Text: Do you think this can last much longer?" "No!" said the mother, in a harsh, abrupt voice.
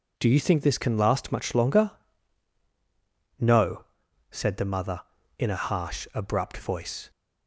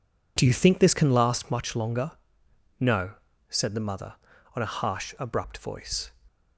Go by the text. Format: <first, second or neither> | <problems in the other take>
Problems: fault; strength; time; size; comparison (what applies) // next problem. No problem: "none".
first | says "on" for "in"; at 4.5 s